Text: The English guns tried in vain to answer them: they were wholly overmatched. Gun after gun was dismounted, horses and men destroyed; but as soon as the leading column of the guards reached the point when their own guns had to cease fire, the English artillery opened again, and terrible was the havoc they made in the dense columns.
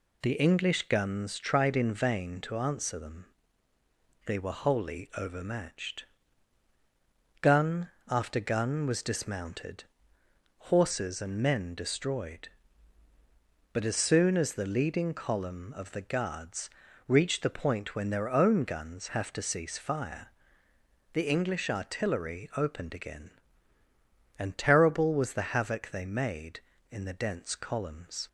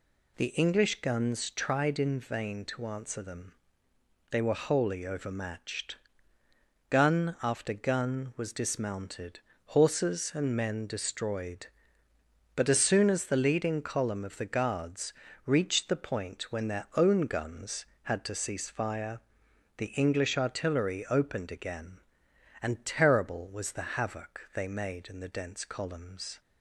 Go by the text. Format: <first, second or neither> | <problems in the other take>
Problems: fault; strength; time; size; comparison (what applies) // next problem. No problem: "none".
second | pauses between "Gun" and "after"; slight; at 7.8 s; 0.18 s long // pauses between "guards" and "reached"; at 16.6 s; 0.38 s long; slight in the second // says "have" for "had"; at 19.1 s